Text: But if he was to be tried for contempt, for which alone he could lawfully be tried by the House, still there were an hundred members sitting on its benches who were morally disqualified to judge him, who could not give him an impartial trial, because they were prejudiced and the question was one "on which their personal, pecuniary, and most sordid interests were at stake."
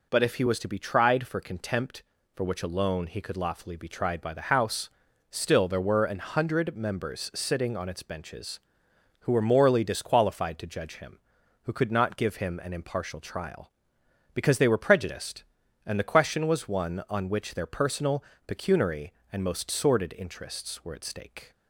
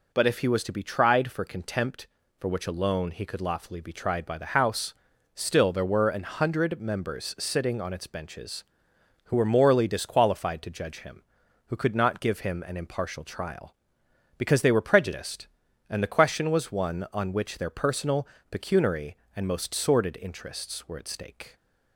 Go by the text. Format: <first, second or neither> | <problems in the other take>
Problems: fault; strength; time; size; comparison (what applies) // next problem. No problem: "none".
neither | none